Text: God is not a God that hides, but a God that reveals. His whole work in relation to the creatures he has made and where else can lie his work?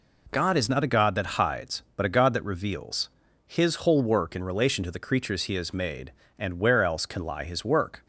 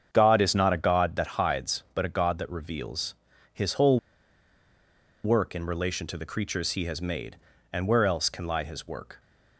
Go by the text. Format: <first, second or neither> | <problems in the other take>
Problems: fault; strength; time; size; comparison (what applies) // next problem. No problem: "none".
first | starts louder than the rest; strong; until 1.1 s; 7.5 dB // pauses between "whole" and "work"; strong; at 3.9 s; 1.2 s long